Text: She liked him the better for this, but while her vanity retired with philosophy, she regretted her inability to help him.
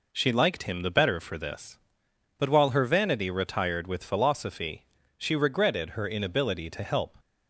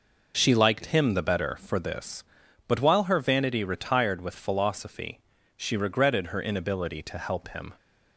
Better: second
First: stops before "him"; at 7.1 s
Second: none

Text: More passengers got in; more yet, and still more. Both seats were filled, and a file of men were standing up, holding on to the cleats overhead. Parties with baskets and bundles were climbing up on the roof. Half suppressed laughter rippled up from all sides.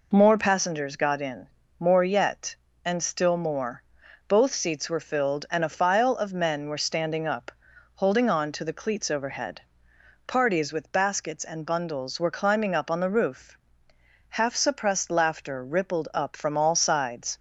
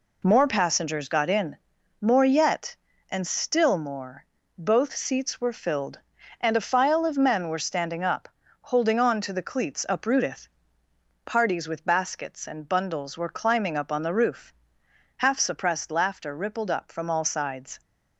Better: first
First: none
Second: says "uprooteth" for "overhead"; at 9.8 s

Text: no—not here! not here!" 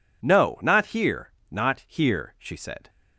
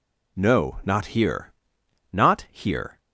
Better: second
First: goes on to say "she said"; from 2.3 s on; 0.52 s long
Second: none

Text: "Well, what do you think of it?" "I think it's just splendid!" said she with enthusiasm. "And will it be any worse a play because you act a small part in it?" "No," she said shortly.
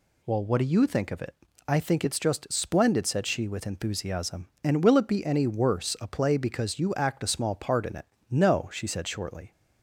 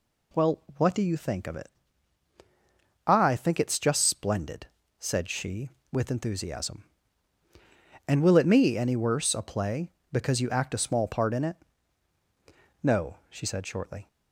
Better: first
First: none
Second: says "me" for "be"; at 8.4 s

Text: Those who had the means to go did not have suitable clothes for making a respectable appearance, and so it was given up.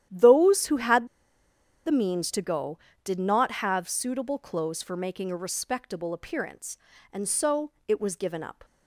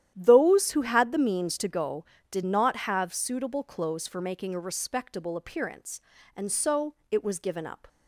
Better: second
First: starts louder than the rest; strong; until 1.9 s; 11 dB // pauses between "had" and "the"; noticeable; at 1.0 s; 0.79 s long // pauses between "so" and "it"; slight; at 7.7 s; 0.16 s long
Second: starts louder than the rest; strong; until 1.1 s; 11 dB // pauses between "so" and "it"; slight; at 6.9 s; 0.16 s long

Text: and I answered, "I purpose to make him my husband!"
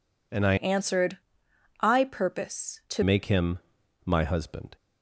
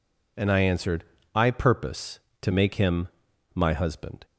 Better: second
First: changes voice from "answered" to "to"; from 0.5 to 3.0 s; 2.5 s long // pauses between "him" and "my"; at 3.5 s; 0.44 s long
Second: pauses between "him" and "my"; at 3.0 s; 0.44 s long

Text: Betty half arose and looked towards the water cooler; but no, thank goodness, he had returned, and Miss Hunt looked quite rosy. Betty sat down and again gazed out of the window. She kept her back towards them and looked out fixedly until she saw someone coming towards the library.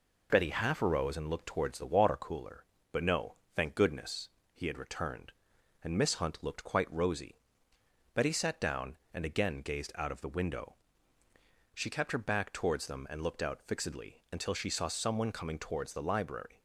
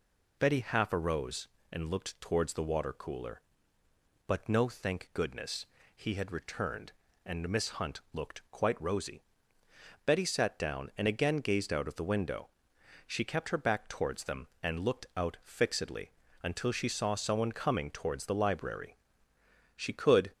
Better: first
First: none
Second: pauses between "fixedly" and "until"; slight; at 16.1 s; 0.32 s long // goes on to say "She could"; from 19.7 s on; 0.54 s long

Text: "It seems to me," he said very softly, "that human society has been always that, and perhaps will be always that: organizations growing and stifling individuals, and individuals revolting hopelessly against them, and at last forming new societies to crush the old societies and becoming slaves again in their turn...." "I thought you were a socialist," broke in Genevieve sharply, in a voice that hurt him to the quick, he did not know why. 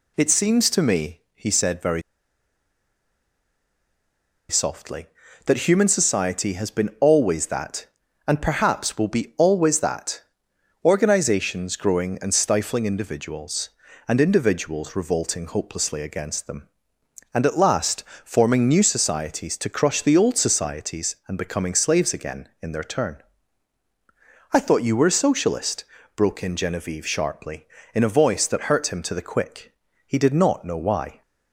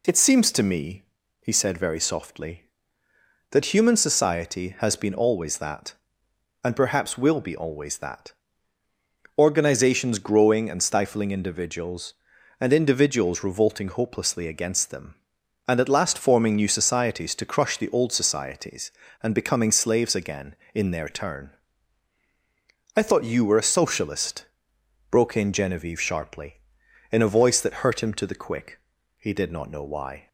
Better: second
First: pauses between "very" and "softly"; strong; at 2.0 s; 2.4 s long // pauses between "last" and "forming"; slight; at 18.0 s; 0.22 s long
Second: none

